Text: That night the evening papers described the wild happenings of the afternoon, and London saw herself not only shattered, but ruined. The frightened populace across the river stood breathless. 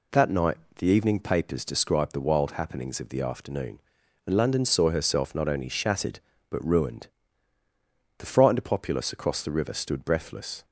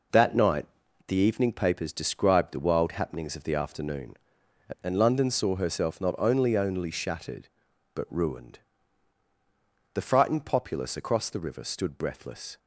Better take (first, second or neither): first